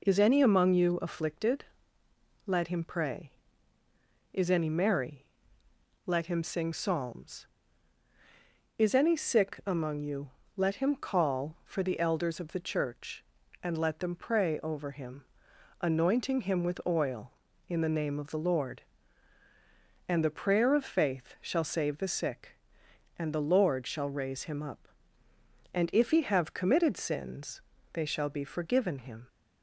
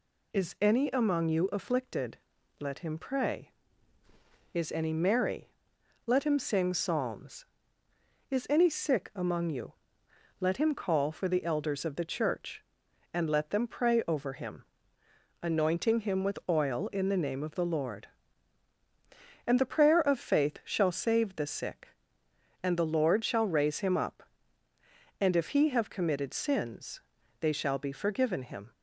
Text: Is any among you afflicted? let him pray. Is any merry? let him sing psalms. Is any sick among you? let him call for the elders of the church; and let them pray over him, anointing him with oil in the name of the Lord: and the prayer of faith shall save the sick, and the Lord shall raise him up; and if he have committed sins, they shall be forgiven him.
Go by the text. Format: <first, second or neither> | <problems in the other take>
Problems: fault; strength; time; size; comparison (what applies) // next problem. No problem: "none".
neither | none